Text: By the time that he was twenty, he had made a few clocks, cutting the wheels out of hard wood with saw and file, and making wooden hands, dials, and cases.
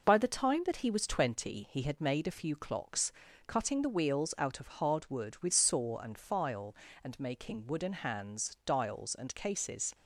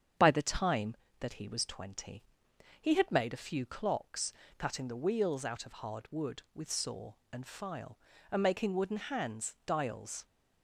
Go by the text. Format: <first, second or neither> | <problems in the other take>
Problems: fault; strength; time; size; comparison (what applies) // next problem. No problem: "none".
first | starts louder than the rest; strong; until 1.4 s; 8 dB // stops before "and cases"; at 10.2 s